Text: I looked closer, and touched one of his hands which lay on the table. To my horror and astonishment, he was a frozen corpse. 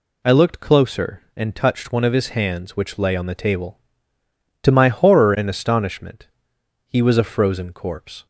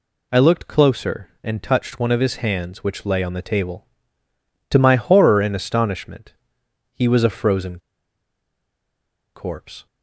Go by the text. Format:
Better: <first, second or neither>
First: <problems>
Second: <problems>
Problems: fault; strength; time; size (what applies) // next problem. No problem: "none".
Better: first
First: none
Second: pauses between "frozen" and "corpse"; strong; at 7.7 s; 1.5 s long